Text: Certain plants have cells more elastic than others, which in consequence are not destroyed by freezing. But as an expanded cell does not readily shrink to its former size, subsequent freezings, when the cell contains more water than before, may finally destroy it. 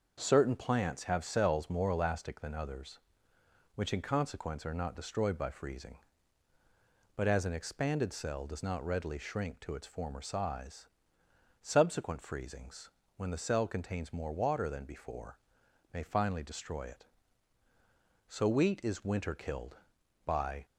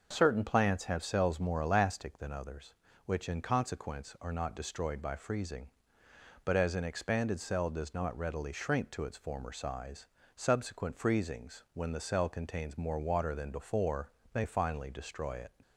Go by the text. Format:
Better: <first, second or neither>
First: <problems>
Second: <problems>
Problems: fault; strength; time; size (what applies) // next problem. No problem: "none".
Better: second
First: starts louder than the rest; until 1.2 s; 6.5 dB // goes on to say "So wheat is winter killed by"; strong; from 18.2 s on; 2.3 s long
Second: starts louder than the rest; noticeable; until 1.1 s; 6 dB